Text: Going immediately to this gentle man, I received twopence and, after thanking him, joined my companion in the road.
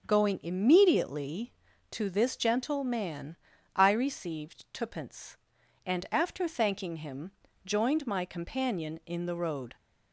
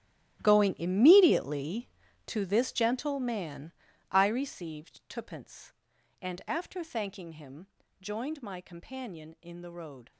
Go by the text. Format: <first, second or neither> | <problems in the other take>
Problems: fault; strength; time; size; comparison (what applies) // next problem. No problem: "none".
first | gets quieter; strong; throughout; 15.5 dB // starts louder than the rest; strong; until 1.4 s; 13.5 dB; also in the first